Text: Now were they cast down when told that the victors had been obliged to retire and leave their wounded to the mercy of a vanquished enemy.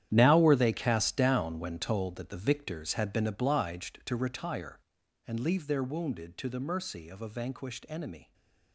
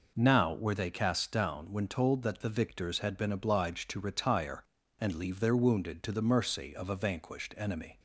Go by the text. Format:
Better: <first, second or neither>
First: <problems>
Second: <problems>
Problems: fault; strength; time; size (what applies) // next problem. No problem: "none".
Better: second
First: gets quieter; strong; throughout; 14.5 dB // stays silent after the last word; slight; from 8.2 s on; 0.5 s long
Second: none